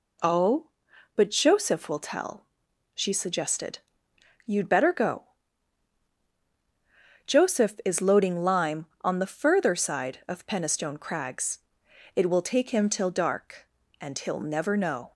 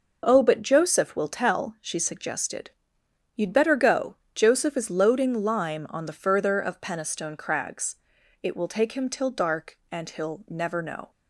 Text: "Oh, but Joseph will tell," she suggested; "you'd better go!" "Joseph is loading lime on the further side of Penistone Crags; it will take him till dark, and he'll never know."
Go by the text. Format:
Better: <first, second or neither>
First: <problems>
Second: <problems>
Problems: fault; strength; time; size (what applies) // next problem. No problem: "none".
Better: first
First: none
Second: skips "side"; at 6.6 s